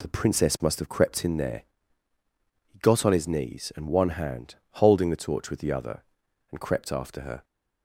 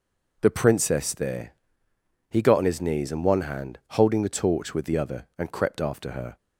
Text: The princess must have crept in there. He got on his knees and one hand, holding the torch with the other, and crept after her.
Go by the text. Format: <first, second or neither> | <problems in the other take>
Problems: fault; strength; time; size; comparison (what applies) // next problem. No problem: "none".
first | skips "must have crept in"; at 1.1 s